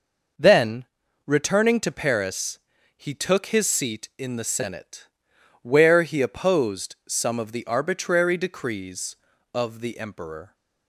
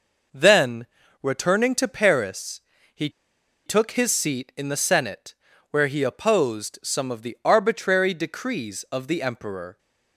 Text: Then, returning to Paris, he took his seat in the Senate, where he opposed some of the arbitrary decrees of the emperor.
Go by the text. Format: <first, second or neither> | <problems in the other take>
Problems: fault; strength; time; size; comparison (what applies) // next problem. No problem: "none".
first | pauses between "he" and "took"; noticeable; at 3.0 s; 0.56 s long